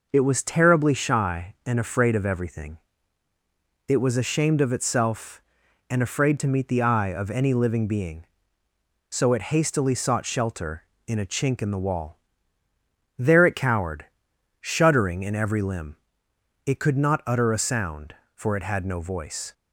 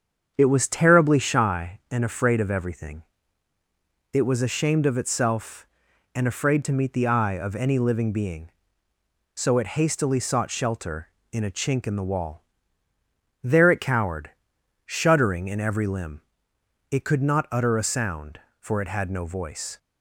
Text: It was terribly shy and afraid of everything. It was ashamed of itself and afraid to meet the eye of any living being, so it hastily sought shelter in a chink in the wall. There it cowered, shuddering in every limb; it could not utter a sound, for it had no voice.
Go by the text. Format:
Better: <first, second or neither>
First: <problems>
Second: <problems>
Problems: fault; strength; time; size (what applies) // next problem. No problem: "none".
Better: first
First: none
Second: starts louder than the rest; strong; until 1.5 s; 7.5 dB